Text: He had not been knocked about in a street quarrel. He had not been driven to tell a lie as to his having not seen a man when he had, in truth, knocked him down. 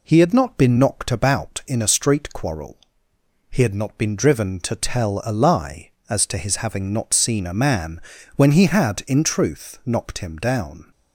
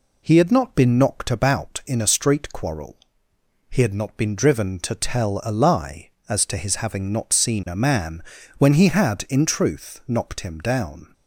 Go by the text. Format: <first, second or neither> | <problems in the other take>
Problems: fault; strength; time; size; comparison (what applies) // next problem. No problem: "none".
neither | pauses between "man" and "when"; slight; the same in both